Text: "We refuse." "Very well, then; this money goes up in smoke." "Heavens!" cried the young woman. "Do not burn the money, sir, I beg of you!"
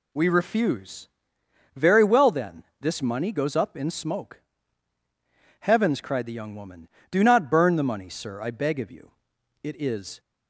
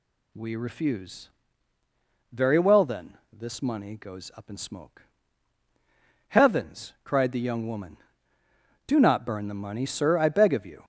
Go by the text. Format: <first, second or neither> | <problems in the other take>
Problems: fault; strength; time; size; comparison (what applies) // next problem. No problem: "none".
second | goes on to say "It is"; from 9.6 s on; 0.58 s long